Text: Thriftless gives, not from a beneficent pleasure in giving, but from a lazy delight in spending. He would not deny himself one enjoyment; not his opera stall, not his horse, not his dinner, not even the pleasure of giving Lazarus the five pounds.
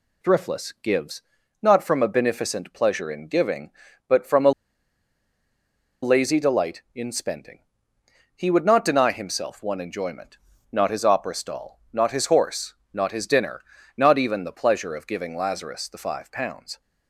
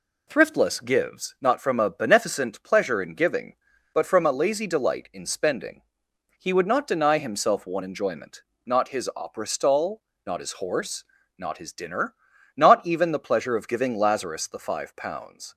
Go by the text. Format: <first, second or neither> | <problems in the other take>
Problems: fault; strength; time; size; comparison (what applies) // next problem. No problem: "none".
second | pauses between "a" and "lazy"; strong; at 4.5 s; 1.5 s long